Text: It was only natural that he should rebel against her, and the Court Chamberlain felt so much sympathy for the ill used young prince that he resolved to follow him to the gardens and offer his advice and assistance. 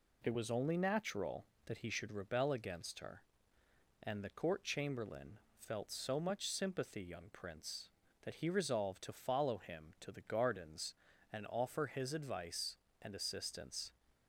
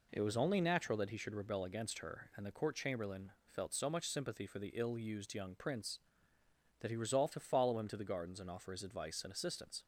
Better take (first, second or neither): second